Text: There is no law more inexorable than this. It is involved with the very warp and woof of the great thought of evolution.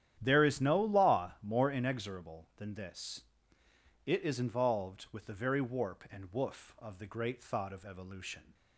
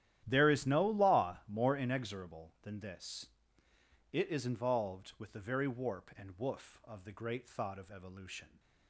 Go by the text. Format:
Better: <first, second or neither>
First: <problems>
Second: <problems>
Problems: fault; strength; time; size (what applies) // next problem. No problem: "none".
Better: first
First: starts louder than the rest; strong; until 1.2 s; 10.5 dB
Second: gets quieter; strong; throughout; 17.5 dB // starts louder than the rest; strong; until 1.2 s; 12 dB